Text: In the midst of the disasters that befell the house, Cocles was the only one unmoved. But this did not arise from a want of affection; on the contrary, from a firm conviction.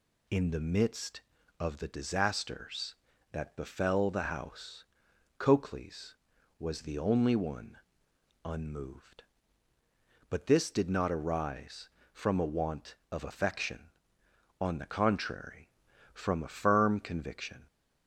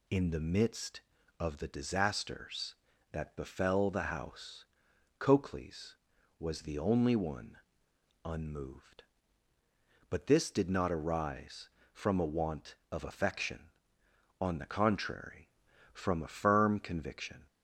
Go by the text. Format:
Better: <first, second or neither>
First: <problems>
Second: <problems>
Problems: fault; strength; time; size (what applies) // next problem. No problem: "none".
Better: neither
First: pauses between "one" and "unmoved"; noticeable; at 7.7 s; 0.66 s long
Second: pauses between "one" and "unmoved"; noticeable; at 7.5 s; 0.66 s long